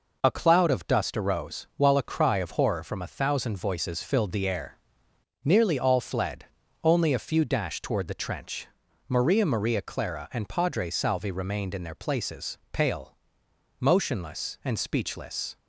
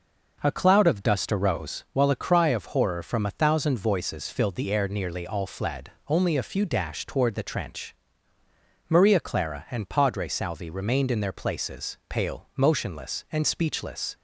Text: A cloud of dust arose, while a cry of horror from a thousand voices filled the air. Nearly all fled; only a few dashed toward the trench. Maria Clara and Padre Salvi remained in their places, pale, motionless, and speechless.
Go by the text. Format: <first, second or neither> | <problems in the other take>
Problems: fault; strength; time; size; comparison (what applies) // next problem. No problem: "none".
second | says "Maria" twice; at 9.4 s